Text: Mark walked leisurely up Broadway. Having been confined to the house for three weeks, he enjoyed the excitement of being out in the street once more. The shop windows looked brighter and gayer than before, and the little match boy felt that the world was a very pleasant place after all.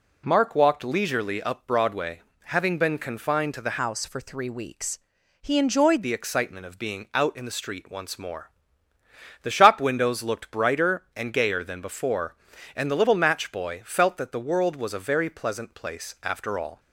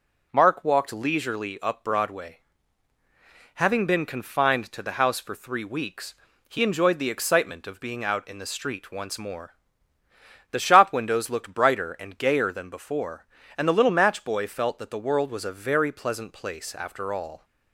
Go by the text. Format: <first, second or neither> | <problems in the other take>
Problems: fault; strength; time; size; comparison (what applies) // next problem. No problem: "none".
second | changes voice from "house" to "enjoyed"; from 3.8 to 6.0 s; 2.2 s long